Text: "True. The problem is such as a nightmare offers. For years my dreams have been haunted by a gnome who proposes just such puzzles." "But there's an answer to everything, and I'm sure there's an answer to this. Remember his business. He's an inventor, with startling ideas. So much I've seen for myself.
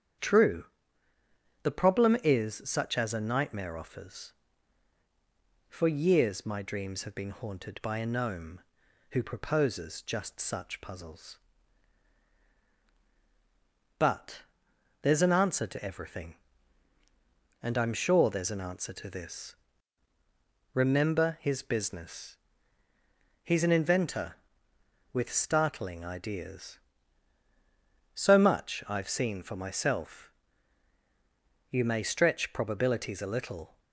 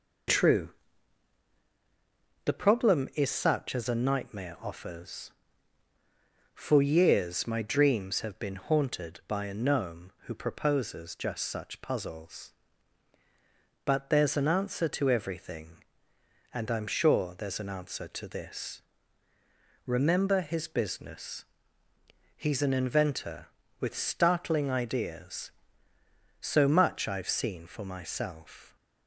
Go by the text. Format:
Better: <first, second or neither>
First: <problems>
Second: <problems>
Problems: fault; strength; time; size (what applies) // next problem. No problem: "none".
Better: second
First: starts louder than the rest; strong; until 2.2 s; 8.5 dB // pauses between "But" and "there's"; noticeable; at 14.4 s; 0.60 s long // goes on to say "You may stretch probabilities a little"; strong; from 31.7 s on; 2.0 s long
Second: none